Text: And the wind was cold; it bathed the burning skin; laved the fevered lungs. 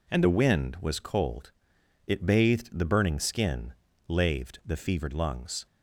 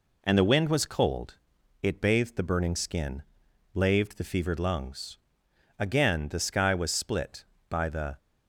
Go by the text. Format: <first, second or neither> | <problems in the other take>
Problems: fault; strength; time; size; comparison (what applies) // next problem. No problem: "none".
first | goes on to say "Again the sky was split by the"; strong; from 5.7 s on; 2.3 s long